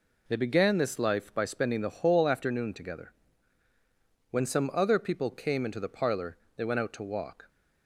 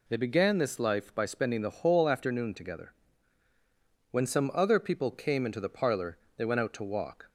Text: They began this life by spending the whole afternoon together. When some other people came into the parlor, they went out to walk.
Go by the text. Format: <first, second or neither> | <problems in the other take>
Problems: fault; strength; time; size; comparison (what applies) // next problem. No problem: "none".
second | gets quieter; throughout; 6.5 dB